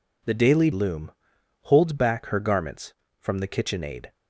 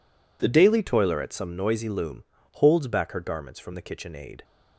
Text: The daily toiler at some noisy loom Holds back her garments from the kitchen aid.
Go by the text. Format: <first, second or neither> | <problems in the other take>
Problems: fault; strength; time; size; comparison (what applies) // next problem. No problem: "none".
second | skips "toiler at some noisy"; at 0.7 s // pauses between "loom" and "Holds"; noticeable; at 1.1 s; 0.52 s long; slight in the second